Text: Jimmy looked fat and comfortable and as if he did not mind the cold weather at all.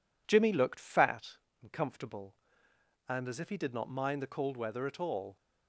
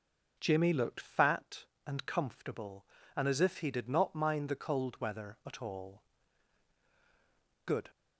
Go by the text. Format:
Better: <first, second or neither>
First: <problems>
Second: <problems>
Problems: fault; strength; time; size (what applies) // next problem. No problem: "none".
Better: first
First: none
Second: goes on to say "Good"; slight; from 7.6 s on; 0.24 s long